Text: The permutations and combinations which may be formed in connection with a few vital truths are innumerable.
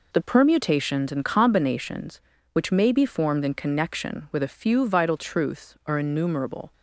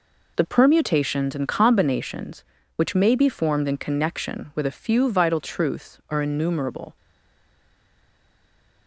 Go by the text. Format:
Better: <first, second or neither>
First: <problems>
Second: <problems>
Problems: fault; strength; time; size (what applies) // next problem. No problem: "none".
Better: first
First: none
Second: stays silent after the last word; noticeable; from 6.9 s on; 1.9 s long